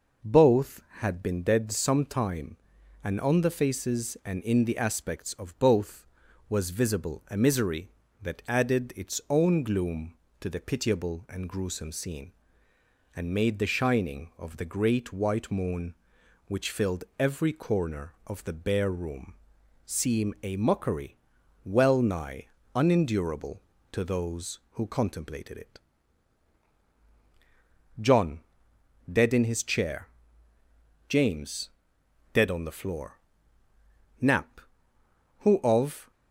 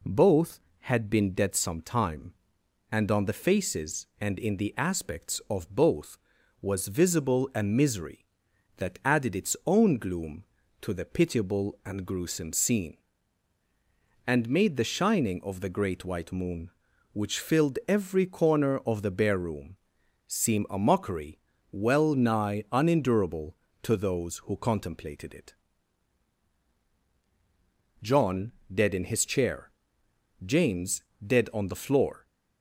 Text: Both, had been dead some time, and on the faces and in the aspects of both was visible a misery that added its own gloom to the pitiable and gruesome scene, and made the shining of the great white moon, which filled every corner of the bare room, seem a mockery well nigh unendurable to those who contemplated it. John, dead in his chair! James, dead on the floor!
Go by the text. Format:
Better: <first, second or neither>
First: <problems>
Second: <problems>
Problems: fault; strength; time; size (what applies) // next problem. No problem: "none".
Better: second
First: pauses between "filled" and "every"; slight; at 17.0 s; 0.16 s long // pauses between "mockery" and "well"; noticeable; at 21.1 s; 0.48 s long // pauses between "nigh" and "unendurable"; slight; at 22.4 s; 0.28 s long // goes on to say "Knapp who of"; strong; from 34.2 s on; 1.9 s long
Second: pauses between "mockery" and "well"; slight; at 21.3 s; 0.32 s long